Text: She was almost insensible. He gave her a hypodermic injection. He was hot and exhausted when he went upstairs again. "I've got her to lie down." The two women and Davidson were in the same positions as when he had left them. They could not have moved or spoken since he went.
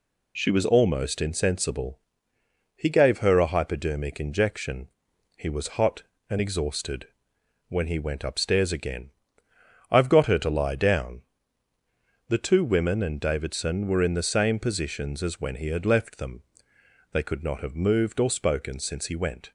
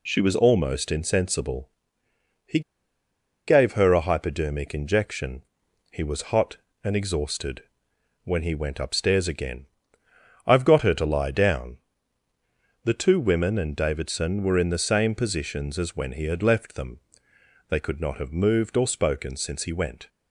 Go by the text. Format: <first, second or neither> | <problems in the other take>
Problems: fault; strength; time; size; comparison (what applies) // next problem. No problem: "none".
first | pauses between "He" and "gave"; noticeable; at 2.6 s; 0.87 s long // pauses between "exhausted" and "when"; noticeable; at 7.6 s; 0.62 s long; noticeable in the first